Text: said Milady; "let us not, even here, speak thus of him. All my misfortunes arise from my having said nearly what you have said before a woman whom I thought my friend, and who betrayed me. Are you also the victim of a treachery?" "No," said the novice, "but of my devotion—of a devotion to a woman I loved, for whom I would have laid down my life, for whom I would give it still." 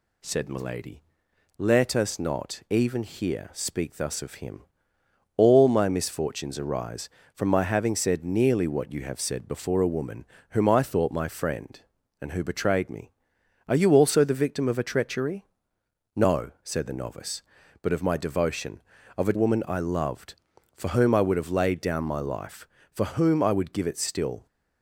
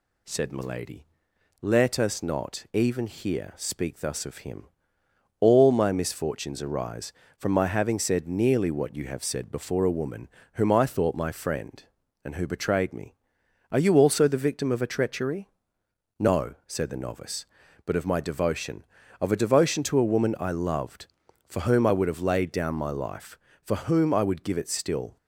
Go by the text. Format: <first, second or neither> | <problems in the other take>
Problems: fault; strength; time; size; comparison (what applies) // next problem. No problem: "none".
second | pauses between "woman" and "whom"; slight; at 10.2 s; 0.26 s long; slight in the second // skips "devotion to a"; at 19.3 s